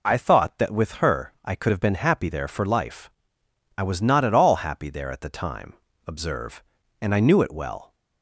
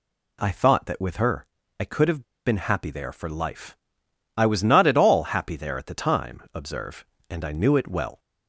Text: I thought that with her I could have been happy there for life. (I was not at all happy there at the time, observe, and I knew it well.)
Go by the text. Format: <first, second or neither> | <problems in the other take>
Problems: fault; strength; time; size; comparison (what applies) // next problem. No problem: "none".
first | pauses between "her" and "I"; slight; at 1.4 s; 0.34 s long // pauses between "have" and "been"; slight; at 2.2 s; 0.22 s long